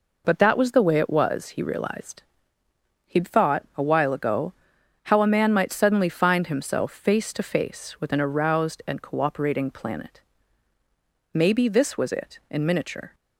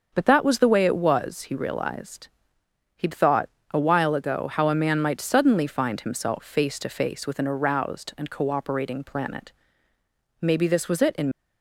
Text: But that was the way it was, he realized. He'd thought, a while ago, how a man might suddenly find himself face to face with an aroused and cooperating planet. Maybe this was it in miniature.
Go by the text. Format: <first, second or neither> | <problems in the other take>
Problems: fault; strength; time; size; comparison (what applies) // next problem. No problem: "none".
first | starts louder than the rest; until 1.1 s; 6.5 dB // stops before "miniature"; at 11.3 s